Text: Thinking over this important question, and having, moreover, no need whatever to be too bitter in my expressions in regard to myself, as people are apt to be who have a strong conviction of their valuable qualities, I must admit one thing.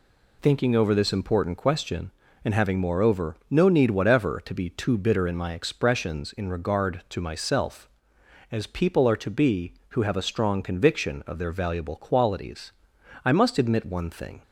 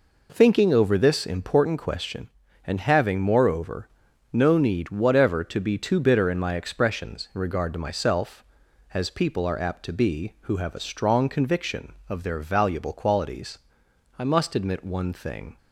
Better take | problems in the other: second | skips "apt"; at 9.1 s

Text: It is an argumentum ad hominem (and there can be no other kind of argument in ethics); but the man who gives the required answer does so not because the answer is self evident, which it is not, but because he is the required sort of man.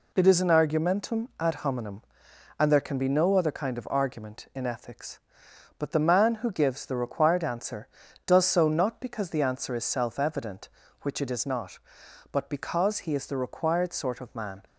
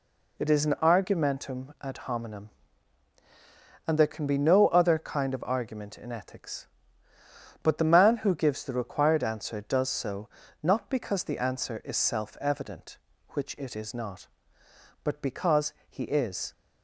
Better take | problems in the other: first | pauses between "so" and "not"; slight; at 10.2 s; 0.34 s long // pauses between "because" and "he"; slight; at 15.7 s; 0.16 s long // stops before "the required sort of man"; at 16.5 s

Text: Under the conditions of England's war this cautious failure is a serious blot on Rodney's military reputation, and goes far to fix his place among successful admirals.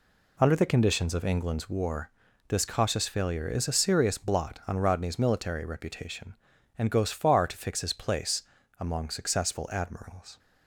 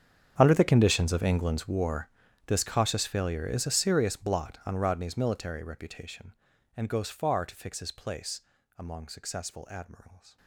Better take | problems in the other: first | gets quieter; strong; throughout; 20 dB // pauses between "war" and "this"; slight; at 2.0 s; 0.36 s long; slight in the first // pauses between "place" and "among"; slight; at 8.4 s; 0.36 s long; slight in the first

